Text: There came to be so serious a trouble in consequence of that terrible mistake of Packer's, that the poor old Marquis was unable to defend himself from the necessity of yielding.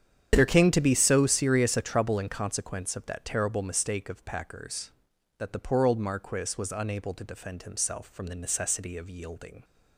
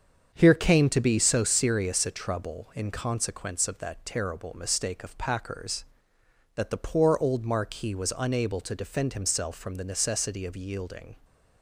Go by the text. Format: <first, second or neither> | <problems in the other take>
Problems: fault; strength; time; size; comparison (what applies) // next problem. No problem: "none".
first | starts louder than the rest; strong; until 1.3 s; 7 dB; strong in the first // says "Here" for "There"; at 0.3 s